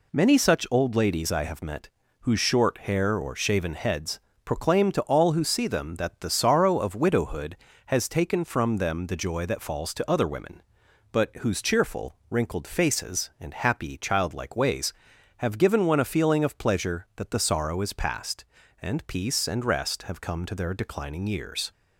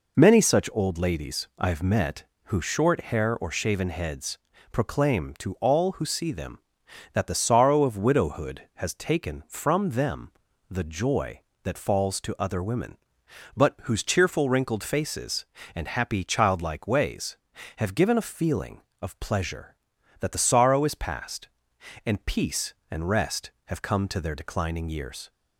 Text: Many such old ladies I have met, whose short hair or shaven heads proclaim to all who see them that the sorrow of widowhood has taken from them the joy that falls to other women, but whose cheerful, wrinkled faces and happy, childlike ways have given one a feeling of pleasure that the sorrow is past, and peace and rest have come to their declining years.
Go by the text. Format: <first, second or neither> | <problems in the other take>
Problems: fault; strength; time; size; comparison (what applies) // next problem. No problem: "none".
first | pauses between "heads" and "proclaim"; slight; at 4.3 s; 0.32 s long; slight in the first // pauses between "them" and "the"; at 10.3 s; 0.40 s long // skips "one"; at 18.1 s